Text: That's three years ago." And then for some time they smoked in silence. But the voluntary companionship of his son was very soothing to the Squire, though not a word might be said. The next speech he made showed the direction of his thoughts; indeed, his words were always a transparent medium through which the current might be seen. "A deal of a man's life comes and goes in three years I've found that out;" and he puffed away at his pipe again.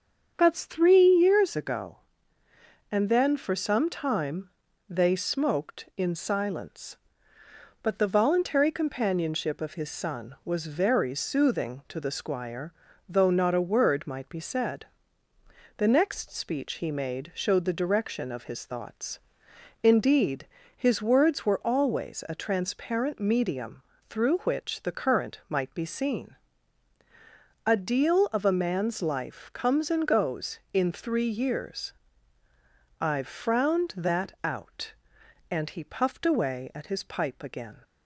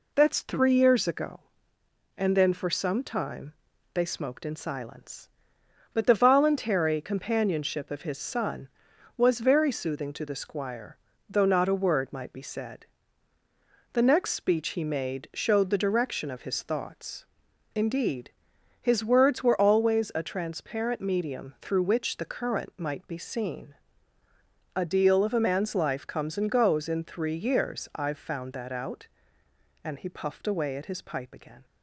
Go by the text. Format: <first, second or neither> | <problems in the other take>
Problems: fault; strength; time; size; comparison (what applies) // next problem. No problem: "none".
second | starts louder than the rest; until 1.3 s; 7 dB // pauses between "time" and "they"; at 4.5 s; 0.38 s long; also in the second // pauses between "medium" and "through"; slight; at 23.8 s; 0.26 s long // pauses between "years" and "I've"; at 31.9 s; 1.0 s long // says "frowned" for "found"; at 33.2 s